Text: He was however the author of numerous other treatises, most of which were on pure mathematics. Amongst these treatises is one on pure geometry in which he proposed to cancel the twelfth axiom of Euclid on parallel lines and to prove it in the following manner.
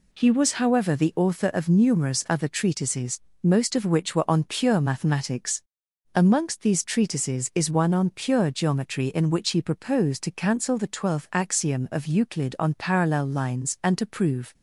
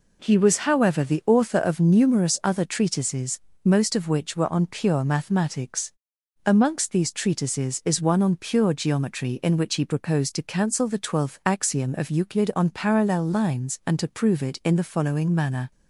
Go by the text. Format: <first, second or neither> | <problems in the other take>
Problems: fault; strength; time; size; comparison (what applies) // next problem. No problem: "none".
second | stops before "it in the following manner"; at 14.5 s